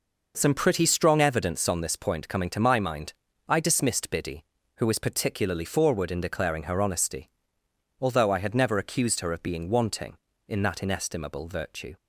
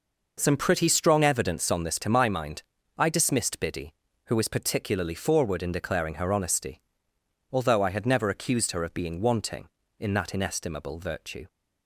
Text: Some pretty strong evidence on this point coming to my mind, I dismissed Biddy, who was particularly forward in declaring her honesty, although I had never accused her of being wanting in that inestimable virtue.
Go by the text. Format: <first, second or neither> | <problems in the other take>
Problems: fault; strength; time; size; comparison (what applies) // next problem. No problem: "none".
first | skips "point coming"; at 1.9 s